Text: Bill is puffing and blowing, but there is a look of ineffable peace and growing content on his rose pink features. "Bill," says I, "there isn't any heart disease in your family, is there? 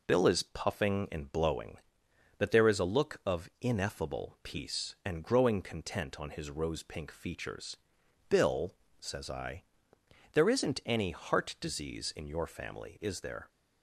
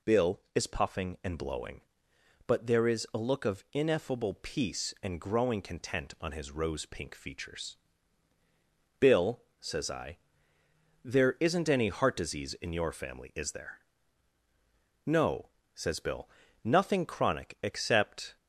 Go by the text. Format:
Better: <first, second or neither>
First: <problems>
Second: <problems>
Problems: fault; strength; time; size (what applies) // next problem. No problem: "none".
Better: first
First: none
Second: goes on to say "No says Bill nothing chronic except"; strong; from 15.0 s on; 3.3 s long